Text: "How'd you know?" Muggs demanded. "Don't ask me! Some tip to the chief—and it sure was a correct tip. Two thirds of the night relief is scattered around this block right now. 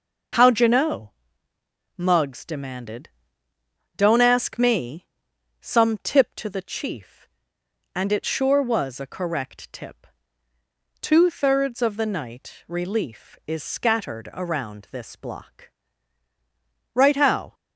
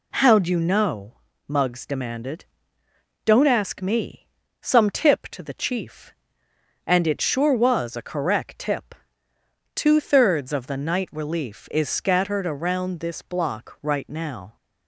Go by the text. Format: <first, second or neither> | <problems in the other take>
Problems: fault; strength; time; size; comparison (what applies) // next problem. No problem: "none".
second | pauses between "block" and "right"; strong; at 15.6 s; 1.2 s long // says "how" for "now"; at 17.1 s